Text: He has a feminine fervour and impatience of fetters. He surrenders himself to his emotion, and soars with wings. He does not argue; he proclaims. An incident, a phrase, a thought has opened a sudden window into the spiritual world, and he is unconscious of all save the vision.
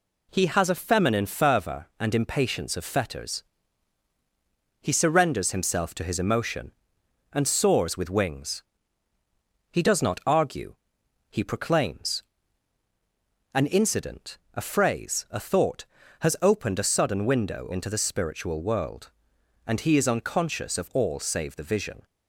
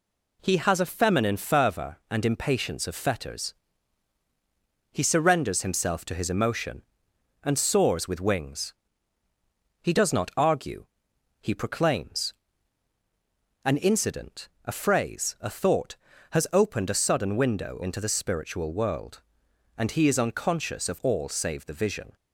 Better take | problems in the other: neither | none

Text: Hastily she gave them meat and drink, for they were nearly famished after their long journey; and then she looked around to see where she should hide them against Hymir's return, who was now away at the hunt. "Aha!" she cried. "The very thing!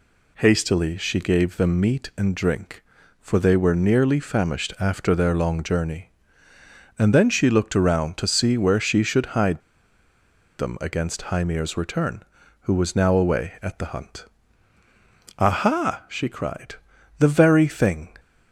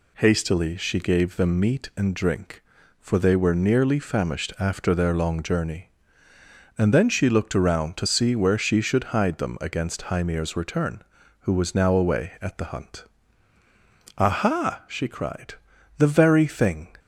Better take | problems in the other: second | pauses between "hide" and "them"; at 9.6 s; 0.98 s long

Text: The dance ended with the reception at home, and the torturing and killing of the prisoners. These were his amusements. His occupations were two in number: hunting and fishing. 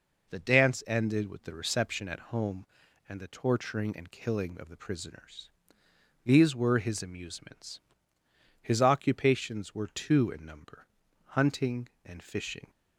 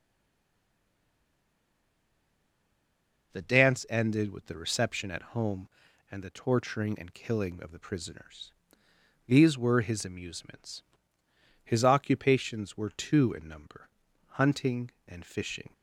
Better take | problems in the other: first | stays silent before the first word; strong; until 3.3 s; 3.3 s long

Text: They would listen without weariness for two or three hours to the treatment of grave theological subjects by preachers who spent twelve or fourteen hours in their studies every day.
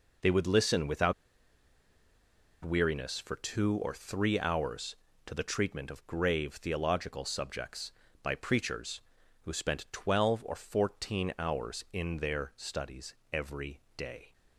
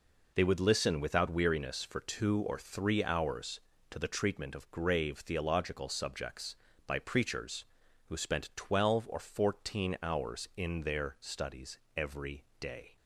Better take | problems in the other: second | pauses between "without" and "weariness"; strong; at 1.1 s; 1.5 s long // pauses between "studies" and "every"; slight; at 13.1 s; 0.18 s long; slight in the second // pauses between "every" and "day"; slight; at 13.8 s; 0.16 s long; slight in the second

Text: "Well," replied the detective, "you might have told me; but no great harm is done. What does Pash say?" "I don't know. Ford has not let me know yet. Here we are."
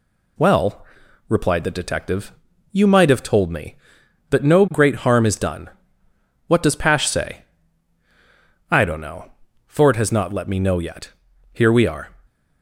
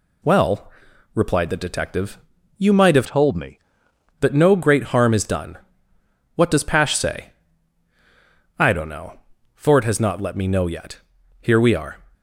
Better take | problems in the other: first | changes voice from "told" to "me"; from 3.0 to 3.5 s; 0.5 s long

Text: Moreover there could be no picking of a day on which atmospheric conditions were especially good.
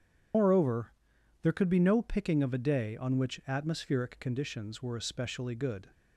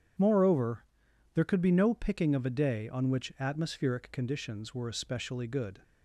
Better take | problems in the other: second | loses the start of "Moreover"; at 0.3 s; 80 ms // starts louder than the rest; strong; until 1.8 s; 8 dB; strong in the second // pauses between "Moreover" and "there"; noticeable; at 0.9 s; 0.52 s long; noticeable in the second

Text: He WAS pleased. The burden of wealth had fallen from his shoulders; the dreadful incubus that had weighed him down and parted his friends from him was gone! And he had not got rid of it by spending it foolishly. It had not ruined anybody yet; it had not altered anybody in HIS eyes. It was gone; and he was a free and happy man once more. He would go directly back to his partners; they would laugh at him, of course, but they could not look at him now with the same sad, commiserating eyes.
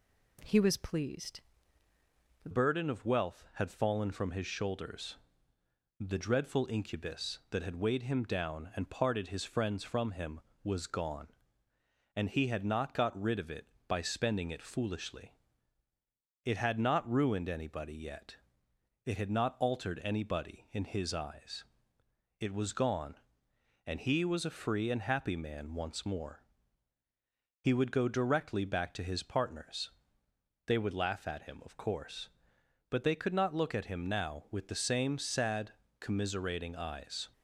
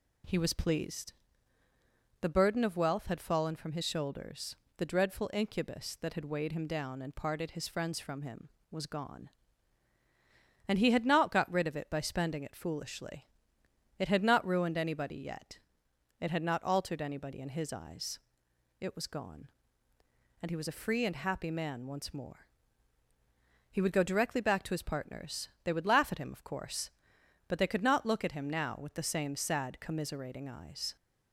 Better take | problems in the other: second | changes voice at "burden"; from 2.5 s on; 34.7 s long

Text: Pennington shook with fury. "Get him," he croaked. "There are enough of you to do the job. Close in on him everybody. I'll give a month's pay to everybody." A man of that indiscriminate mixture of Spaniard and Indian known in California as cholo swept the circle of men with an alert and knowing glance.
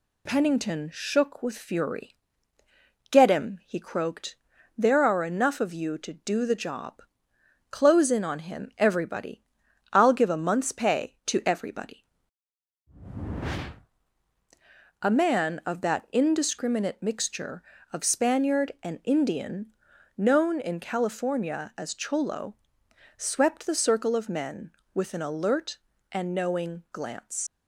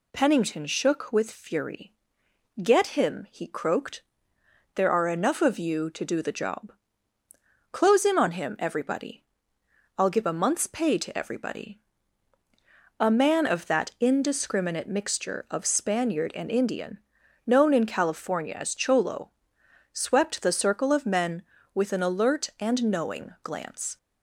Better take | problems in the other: second | pauses between "Indian" and "known"; at 19.7 s; 0.44 s long; noticeable in the second // pauses between "cholo" and "swept"; noticeable; at 22.5 s; 0.64 s long; noticeable in the second // leaves "glance" unfinished; at 27.4 s; 100 ms

